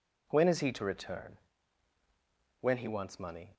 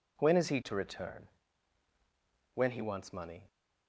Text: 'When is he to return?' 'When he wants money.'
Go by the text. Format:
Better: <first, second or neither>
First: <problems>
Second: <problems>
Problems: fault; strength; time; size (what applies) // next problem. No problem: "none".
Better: neither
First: none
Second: none